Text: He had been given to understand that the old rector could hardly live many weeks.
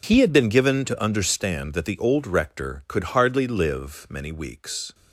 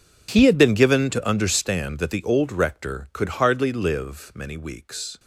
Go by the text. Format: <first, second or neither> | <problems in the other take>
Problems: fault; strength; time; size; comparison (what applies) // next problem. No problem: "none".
first | gets quieter; strong; throughout; 18 dB